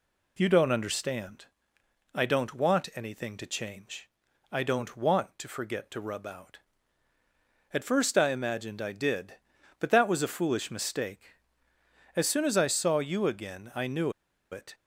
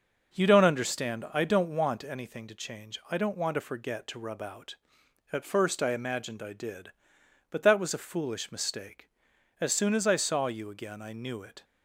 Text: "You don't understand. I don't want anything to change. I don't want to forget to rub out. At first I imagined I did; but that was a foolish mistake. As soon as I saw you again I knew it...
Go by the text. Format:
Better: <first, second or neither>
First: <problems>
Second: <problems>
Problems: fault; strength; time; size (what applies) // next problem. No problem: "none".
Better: second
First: pauses between "knew" and "it"; at 14.1 s; 0.40 s long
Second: none